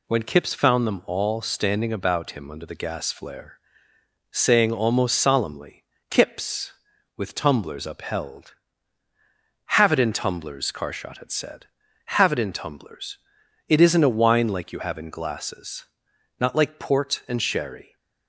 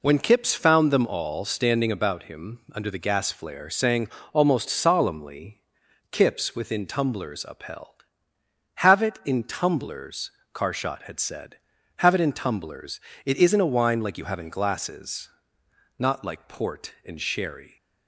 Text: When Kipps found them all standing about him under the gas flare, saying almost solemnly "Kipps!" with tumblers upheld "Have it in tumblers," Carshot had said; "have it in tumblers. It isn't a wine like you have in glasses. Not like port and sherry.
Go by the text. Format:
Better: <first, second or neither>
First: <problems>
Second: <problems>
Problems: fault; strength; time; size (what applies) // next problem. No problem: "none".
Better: first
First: pauses between "solemnly" and "Kipps"; slight; at 5.8 s; 0.28 s long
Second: pauses between "saying" and "almost"; slight; at 4.0 s; 0.24 s long // pauses between "solemnly" and "Kipps"; noticeable; at 5.6 s; 0.50 s long // says "within" for "with"; at 6.5 s